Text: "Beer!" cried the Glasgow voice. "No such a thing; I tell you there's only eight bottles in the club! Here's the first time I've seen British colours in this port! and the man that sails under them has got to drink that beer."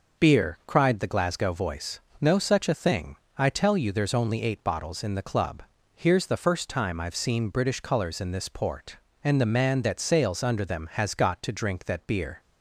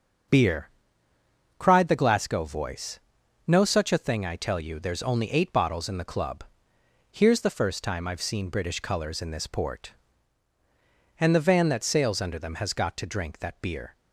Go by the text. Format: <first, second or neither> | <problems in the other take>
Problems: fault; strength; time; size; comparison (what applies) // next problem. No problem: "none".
first | starts louder than the rest; until 2.2 s; 7 dB // says "van" for "man"; at 11.4 s